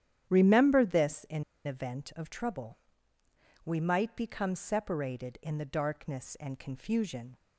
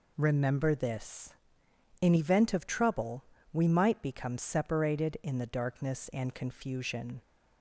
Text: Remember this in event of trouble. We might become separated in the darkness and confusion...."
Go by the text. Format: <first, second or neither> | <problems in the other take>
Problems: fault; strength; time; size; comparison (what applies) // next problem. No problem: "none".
second | starts louder than the rest; strong; until 1.3 s; 10.5 dB // pauses between "in" and "event"; slight; at 1.4 s; 0.22 s long